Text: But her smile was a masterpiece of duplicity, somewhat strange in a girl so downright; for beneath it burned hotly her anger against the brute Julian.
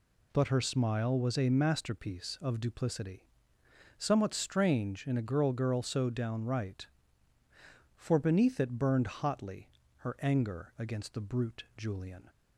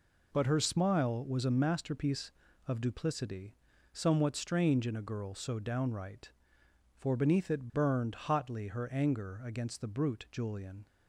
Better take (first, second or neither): second